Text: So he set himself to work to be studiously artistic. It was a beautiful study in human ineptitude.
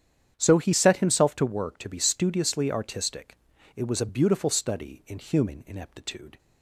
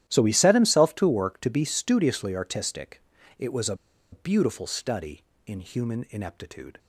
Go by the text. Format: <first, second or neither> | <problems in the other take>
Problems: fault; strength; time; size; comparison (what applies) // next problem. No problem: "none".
first | starts louder than the rest; strong; until 1.0 s; 12.5 dB; strong in the first // pauses between "a" and "beautiful"; at 3.7 s; 0.37 s long